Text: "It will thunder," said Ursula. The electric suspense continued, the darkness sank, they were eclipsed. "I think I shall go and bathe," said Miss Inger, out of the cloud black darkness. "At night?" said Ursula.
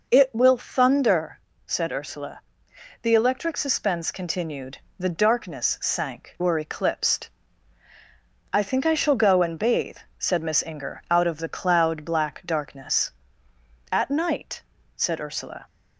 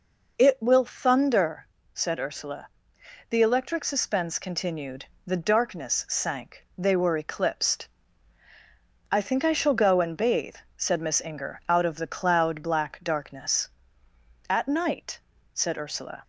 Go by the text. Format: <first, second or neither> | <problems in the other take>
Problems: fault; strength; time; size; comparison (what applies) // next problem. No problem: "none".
second | skips "they"; at 6.3 s